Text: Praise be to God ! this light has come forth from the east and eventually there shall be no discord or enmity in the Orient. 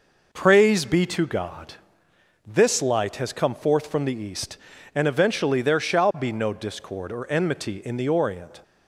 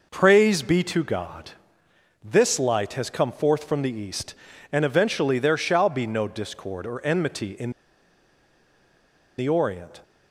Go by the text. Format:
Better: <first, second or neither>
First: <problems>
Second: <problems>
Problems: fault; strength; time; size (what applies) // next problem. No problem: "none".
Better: first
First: none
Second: pauses between "in" and "the"; strong; at 7.7 s; 1.6 s long